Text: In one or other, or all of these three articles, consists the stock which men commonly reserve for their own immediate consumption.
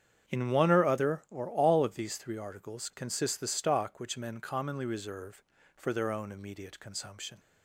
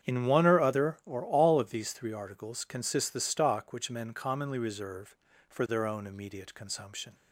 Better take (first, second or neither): neither